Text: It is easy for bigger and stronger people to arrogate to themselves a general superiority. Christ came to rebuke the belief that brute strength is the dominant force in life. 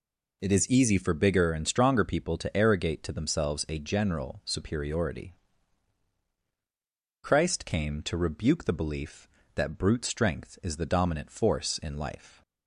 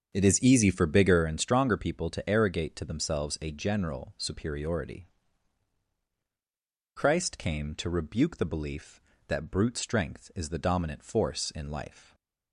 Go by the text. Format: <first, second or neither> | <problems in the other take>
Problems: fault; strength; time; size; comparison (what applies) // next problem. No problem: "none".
first | starts louder than the rest; strong; until 1.4 s; 7.5 dB